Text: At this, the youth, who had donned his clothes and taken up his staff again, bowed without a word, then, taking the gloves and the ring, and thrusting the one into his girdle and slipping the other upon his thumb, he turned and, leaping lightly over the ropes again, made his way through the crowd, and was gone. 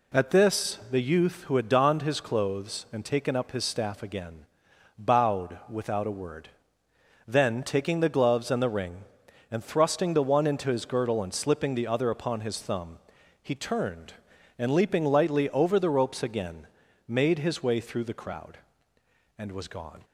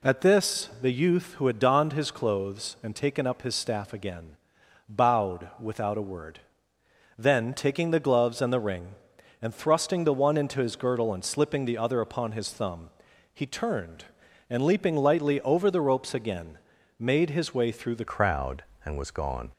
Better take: first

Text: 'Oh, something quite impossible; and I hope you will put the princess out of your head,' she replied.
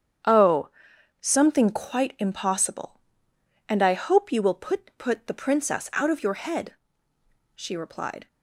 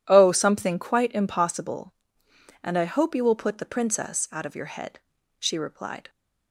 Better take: second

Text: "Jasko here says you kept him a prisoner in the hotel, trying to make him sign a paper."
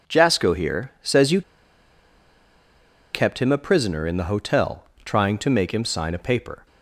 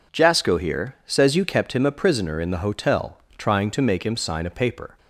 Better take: second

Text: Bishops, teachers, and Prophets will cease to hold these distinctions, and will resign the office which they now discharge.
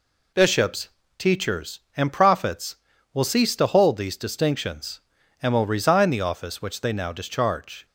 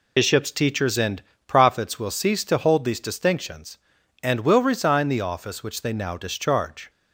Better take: first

